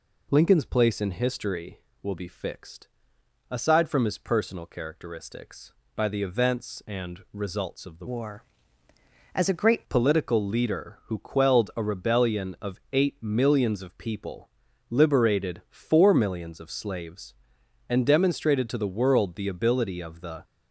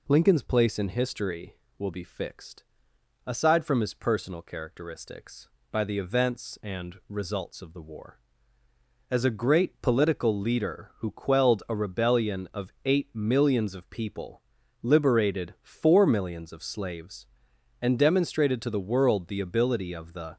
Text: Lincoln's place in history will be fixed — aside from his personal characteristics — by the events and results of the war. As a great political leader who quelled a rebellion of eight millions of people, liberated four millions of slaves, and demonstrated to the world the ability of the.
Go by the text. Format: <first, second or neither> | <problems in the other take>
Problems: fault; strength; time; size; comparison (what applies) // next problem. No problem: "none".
second | changes voice from "war" to "great"; from 8.0 to 9.8 s; 1.8 s long